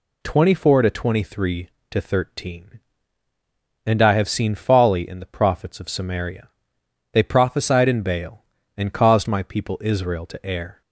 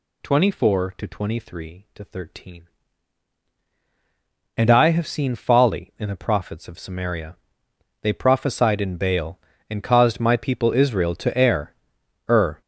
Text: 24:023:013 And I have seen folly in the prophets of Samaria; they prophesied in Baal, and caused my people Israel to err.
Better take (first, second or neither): first